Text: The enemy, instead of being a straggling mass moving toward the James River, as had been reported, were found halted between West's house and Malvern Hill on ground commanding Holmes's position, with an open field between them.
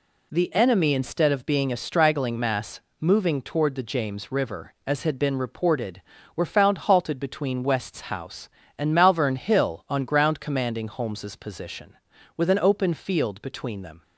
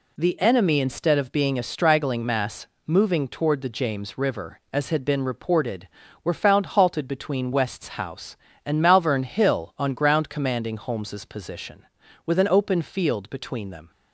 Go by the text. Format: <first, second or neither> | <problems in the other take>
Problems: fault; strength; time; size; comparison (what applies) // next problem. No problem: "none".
neither | pauses between "mass" and "moving"; slight; the same in both